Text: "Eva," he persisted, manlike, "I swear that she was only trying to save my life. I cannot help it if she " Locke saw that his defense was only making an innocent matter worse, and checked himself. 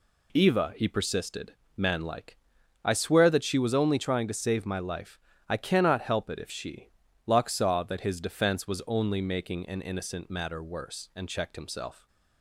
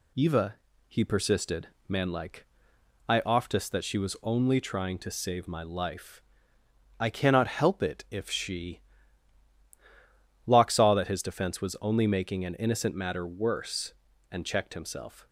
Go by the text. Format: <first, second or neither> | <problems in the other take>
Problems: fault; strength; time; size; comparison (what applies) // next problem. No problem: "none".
first | says "oftest" for "swear"; at 3.2 s